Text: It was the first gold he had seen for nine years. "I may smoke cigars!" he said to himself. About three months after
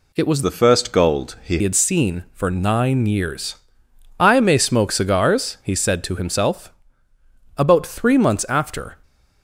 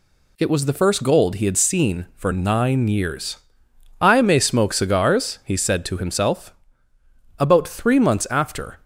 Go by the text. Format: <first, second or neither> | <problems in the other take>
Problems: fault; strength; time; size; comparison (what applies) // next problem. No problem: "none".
second | changes voice from "the" to "he"; from 0.4 to 1.5 s; 1.1 s long